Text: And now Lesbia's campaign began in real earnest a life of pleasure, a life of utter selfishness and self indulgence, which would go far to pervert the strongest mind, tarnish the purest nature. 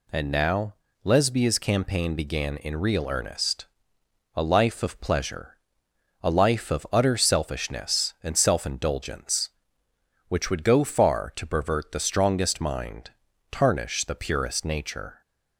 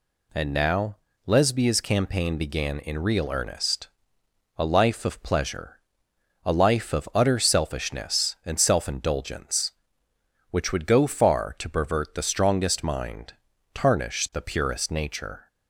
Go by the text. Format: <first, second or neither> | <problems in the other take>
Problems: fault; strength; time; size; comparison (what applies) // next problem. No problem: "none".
neither | pauses between "now" and "Lesbia's"; slight; the same in both // pauses between "earnest" and "a"; noticeable; the same in both